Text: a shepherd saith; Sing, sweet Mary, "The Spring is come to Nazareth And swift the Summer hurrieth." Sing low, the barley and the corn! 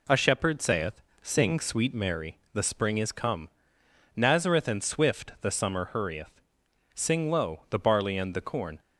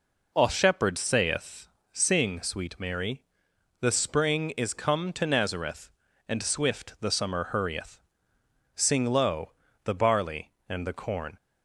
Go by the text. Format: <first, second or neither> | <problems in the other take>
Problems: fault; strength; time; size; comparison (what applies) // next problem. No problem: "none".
second | skips "to"; at 3.8 s